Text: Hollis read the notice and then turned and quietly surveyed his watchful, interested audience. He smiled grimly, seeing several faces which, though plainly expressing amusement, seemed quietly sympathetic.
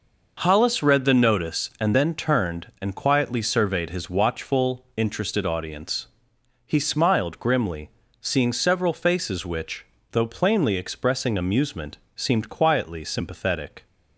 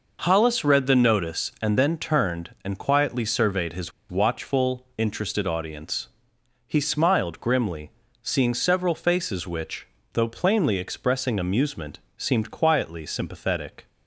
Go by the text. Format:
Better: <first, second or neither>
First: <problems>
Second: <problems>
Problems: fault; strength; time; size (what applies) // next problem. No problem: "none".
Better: first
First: none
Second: pauses between "his" and "watchful"; slight; at 3.9 s; 0.20 s long